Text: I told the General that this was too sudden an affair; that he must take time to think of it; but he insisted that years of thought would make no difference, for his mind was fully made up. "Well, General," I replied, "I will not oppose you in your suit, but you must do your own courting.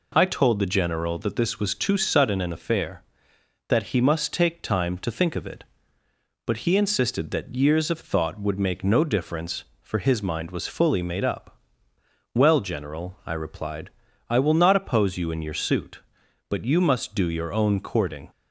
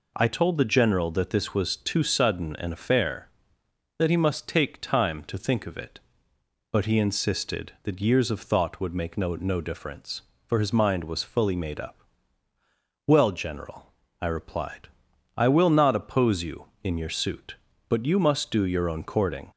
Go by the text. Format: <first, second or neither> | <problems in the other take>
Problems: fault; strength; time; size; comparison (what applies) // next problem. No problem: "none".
first | says "no" twice; at 9.3 s